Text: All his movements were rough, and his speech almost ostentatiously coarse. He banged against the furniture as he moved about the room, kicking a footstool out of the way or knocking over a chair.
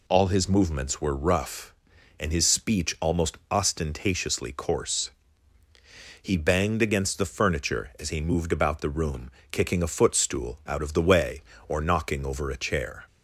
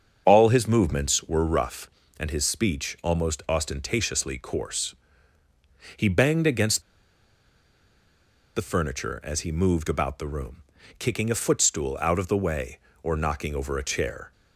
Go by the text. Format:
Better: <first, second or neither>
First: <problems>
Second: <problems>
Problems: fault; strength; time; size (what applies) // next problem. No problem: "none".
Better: first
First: none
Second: starts louder than the rest; until 1.2 s; 7 dB // pauses between "against" and "the"; strong; at 6.8 s; 1.7 s long